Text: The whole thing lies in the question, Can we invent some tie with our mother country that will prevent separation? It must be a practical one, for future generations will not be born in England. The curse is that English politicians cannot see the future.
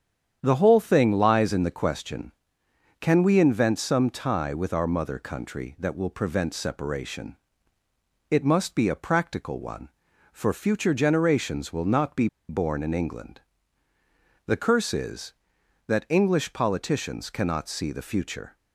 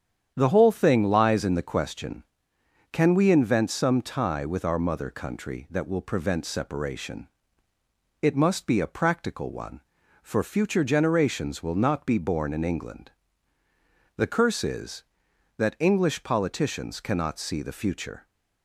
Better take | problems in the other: second | starts louder than the rest; strong; until 1.4 s; 8.5 dB; strong in the second // pauses between "be" and "born"; slight; at 12.2 s; 0.21 s long

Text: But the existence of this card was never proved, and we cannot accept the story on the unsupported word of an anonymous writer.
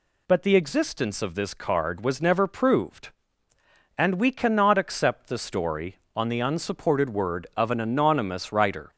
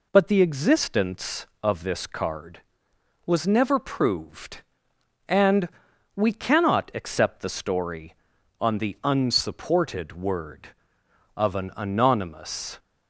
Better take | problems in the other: first | pauses between "and" and "we"; noticeable; at 5.6 s; 0.46 s long // stops before "writer"; at 12.7 s

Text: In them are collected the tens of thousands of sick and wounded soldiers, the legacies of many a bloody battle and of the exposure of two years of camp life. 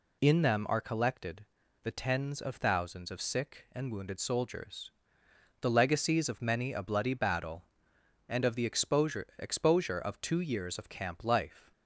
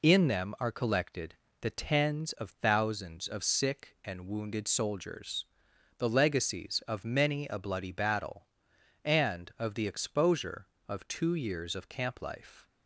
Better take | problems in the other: second | pauses between "collected" and "the"; at 1.4 s; 0.36 s long; slight in the second // says "exposure" twice; at 9.3 s

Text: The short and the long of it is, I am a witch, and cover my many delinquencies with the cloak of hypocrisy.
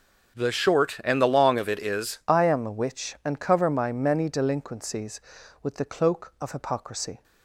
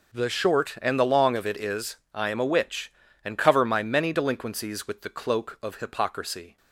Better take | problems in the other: second | starts louder than the rest; strong; until 1.4 s; 7.5 dB // changes voice at "I"; from 2.2 s on; 5.0 s long

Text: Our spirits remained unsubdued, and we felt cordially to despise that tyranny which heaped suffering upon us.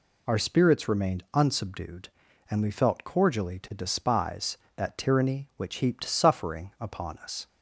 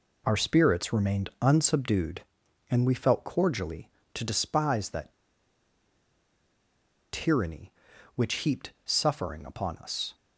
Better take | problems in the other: first | pauses between "that" and "tyranny"; strong; at 5.1 s; 1.9 s long

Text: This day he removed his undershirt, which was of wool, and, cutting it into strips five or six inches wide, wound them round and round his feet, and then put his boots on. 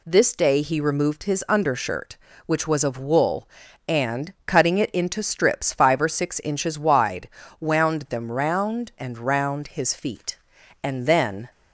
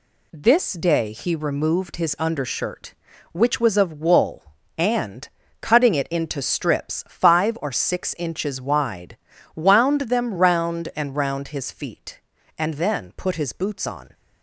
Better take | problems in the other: second | stops before "put his boots on"; at 11.4 s

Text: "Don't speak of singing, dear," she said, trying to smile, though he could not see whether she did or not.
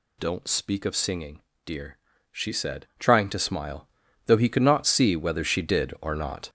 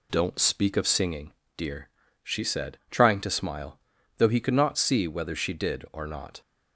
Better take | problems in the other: second | gets louder; strong; throughout; 8 dB

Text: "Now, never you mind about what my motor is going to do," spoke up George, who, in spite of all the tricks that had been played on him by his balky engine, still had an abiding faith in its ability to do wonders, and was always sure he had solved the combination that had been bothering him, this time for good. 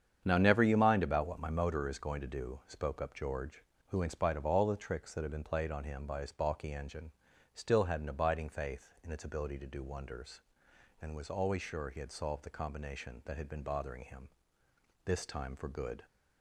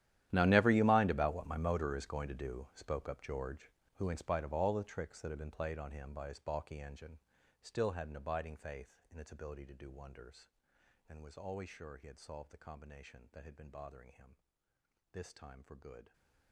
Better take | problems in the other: first | gets quieter; strong; throughout; 20.5 dB // starts louder than the rest; strong; until 1.3 s; 12 dB; strong in the first

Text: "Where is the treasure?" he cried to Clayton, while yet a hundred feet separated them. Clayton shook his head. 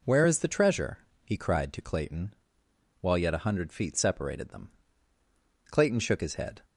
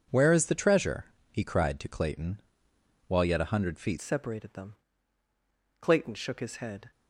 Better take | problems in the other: first | changes voice at "separated"; from 4.0 s on; 2.9 s long

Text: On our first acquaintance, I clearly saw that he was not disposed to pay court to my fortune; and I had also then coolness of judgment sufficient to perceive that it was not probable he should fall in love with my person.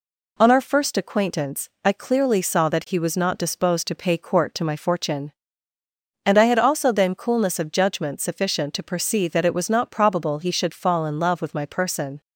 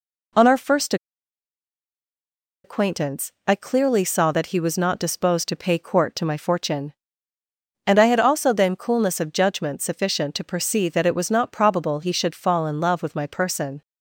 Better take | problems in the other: first | pauses between "first" and "acquaintance"; strong; at 0.9 s; 1.6 s long

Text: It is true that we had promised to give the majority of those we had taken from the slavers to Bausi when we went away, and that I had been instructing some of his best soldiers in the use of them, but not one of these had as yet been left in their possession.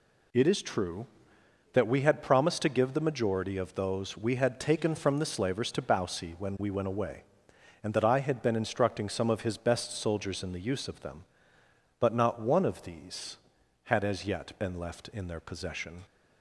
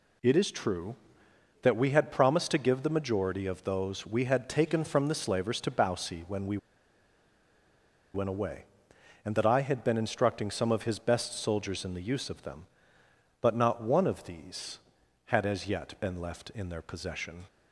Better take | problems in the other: first | pauses between "we" and "went"; strong; at 6.5 s; 1.5 s long

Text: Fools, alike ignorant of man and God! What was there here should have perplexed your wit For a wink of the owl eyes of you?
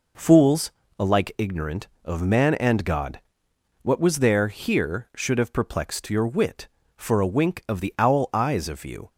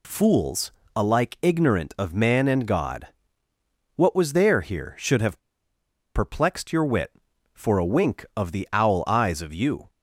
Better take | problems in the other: first | pauses between "have" and "perplexed"; noticeable; at 5.3 s; 0.76 s long

